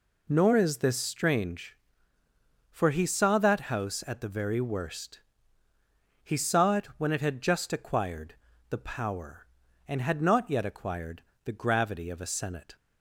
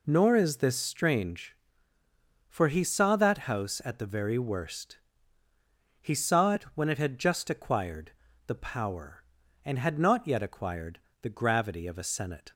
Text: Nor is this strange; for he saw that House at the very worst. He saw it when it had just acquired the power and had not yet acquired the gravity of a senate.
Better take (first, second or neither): neither